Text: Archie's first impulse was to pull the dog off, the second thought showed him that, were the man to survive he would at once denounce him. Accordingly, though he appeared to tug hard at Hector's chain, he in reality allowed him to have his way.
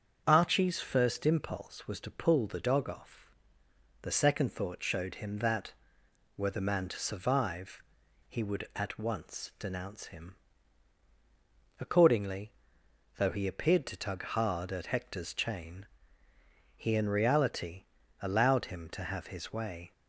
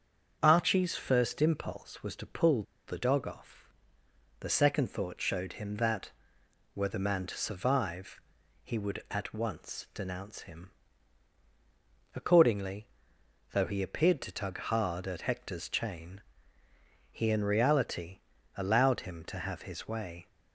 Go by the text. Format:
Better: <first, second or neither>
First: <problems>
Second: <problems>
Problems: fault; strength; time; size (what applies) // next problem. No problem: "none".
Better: first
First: starts louder than the rest; strong; until 1.2 s; 7 dB // pauses between "survive" and "he"; noticeable; at 7.8 s; 0.46 s long // pauses between "reality" and "allowed"; slight; at 17.8 s; 0.36 s long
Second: starts louder than the rest; strong; until 1.4 s; 7 dB // pauses between "pull" and "the"; slight; at 2.6 s; 0.24 s long // pauses between "survive" and "he"; at 8.1 s; 0.44 s long // pauses between "reality" and "allowed"; slight; at 18.1 s; 0.36 s long